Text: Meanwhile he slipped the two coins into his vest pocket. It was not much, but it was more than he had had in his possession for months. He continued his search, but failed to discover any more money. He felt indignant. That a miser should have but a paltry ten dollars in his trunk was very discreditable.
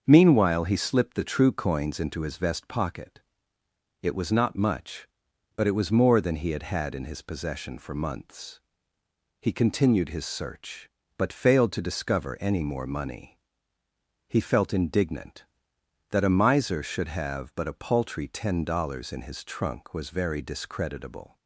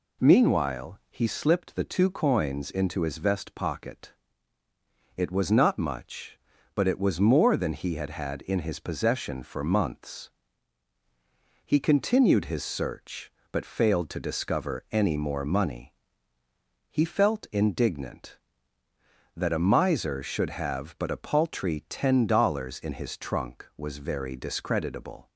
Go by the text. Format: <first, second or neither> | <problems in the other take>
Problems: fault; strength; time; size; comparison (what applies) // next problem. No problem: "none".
second | starts louder than the rest; until 1.0 s; 7 dB // says "true" for "two"; at 1.2 s